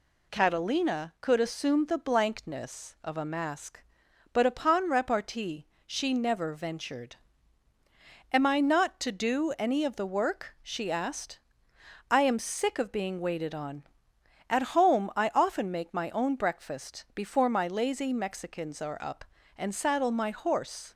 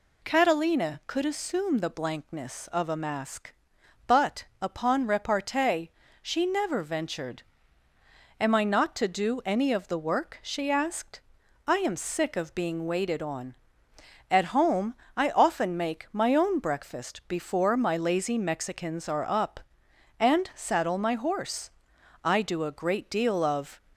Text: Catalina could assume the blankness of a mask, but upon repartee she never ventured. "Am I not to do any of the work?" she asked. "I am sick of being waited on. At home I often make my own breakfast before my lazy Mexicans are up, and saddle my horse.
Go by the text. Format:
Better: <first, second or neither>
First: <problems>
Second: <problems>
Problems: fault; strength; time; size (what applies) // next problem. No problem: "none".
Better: first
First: pauses between "repartee" and "she"; slight; at 5.6 s; 0.22 s long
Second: pauses between "but" and "upon"; slight; at 4.4 s; 0.16 s long // pauses between "repartee" and "she"; slight; at 5.9 s; 0.30 s long // pauses between "home" and "I"; slight; at 14.9 s; 0.22 s long // goes on to say "I do a great deal of"; from 22.2 s on; 1.5 s long